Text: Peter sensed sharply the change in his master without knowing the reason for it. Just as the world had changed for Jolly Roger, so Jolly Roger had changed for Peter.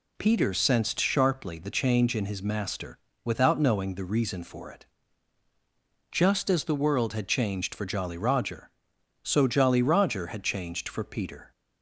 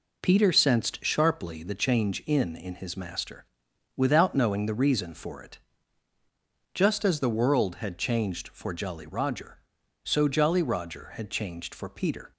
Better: first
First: pauses between "master" and "without"; slight; at 2.9 s; 0.28 s long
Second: says "in" twice; at 2.5 s // pauses between "master" and "without"; noticeable; at 3.4 s; 0.50 s long

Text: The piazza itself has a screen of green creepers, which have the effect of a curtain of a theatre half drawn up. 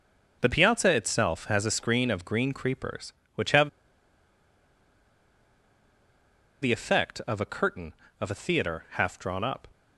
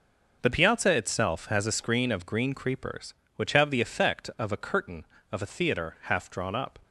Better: second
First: pauses between "have" and "the"; strong; at 3.6 s; 2.9 s long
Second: none

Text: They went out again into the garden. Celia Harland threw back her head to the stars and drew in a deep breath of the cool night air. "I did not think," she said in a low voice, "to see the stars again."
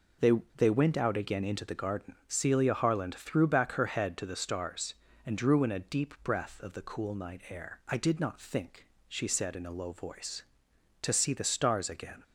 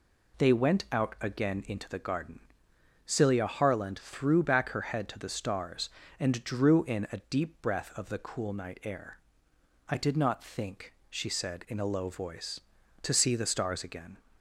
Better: second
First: says "They" twice; at 0.5 s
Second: none

